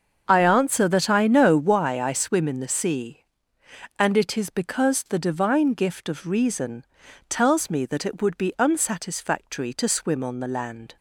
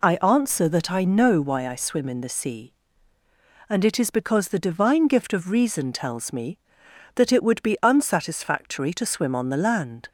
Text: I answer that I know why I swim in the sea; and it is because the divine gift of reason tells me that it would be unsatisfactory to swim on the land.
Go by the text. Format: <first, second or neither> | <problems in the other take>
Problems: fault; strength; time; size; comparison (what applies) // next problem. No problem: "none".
second | starts louder than the rest; until 2.0 s; 6.5 dB // pauses between "reason" and "tells"; at 6.8 s; 0.44 s long